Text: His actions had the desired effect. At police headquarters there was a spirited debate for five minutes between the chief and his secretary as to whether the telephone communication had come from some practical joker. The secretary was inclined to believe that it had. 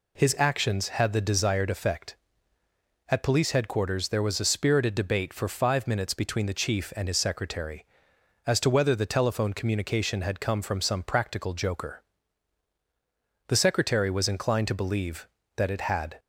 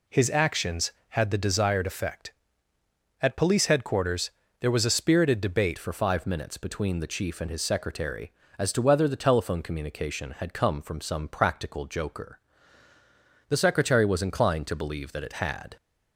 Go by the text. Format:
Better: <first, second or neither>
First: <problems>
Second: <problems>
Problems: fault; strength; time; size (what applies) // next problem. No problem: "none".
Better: first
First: none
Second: pauses between "headquarters" and "there"; slight; at 4.3 s; 0.28 s long // changes voice at "for"; from 5.7 s on; 10.0 s long